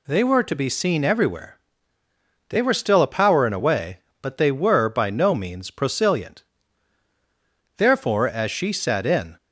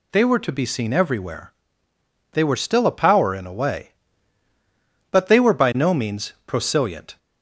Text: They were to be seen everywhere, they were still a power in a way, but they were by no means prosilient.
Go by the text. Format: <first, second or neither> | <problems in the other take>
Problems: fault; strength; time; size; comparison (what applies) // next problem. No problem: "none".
second | goes on to say "Therefore as she sat in"; from 7.7 s on; 1.6 s long